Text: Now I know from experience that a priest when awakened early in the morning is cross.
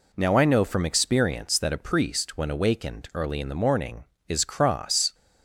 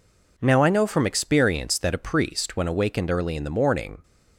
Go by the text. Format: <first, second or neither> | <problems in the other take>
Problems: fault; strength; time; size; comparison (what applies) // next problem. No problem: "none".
first | stops before "is cross"; at 4.0 s